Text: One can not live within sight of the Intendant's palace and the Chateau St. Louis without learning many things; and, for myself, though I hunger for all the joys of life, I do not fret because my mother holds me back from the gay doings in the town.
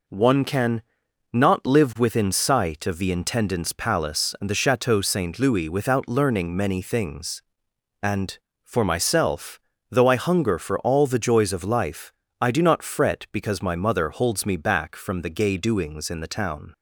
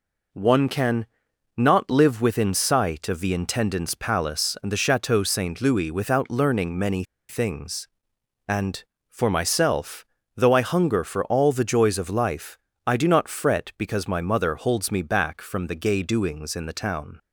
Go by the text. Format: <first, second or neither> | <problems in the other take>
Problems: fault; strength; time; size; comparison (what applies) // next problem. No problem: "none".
first | pauses between "can" and "not"; noticeable; at 1.0 s; 0.50 s long; noticeable in the first // pauses between "many" and "things"; slight; at 7.0 s; 0.26 s long